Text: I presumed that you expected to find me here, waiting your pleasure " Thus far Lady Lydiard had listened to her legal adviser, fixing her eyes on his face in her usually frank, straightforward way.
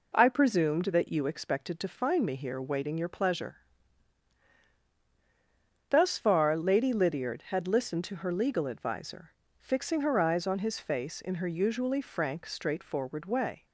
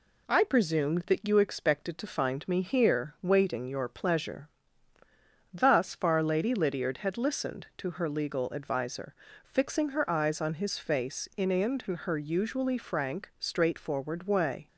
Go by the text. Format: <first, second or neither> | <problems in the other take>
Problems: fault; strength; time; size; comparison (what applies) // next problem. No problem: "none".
first | says "in" twice; at 11.5 s